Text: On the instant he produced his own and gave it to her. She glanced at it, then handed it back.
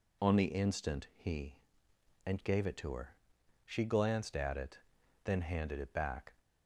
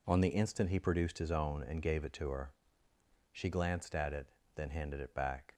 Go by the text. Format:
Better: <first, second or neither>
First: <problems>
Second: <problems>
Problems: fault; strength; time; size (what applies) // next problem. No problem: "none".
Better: second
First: skips "produced his own"; at 1.9 s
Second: none